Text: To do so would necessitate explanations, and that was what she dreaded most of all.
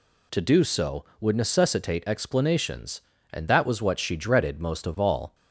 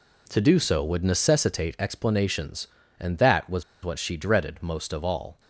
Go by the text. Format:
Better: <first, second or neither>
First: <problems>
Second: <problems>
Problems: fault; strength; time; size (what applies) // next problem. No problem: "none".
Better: first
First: none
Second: pauses between "was" and "what"; slight; at 3.6 s; 0.20 s long